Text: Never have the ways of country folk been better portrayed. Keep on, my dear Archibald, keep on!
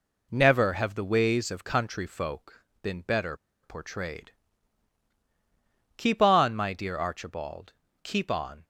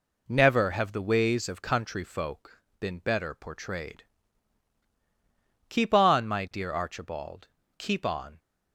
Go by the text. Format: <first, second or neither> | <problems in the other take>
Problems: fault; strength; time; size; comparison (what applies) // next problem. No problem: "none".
second | pauses between "folk" and "been"; slight; at 2.6 s; 0.20 s long; slight in the second // pauses between "better" and "portrayed"; slight; at 3.3 s; 0.28 s long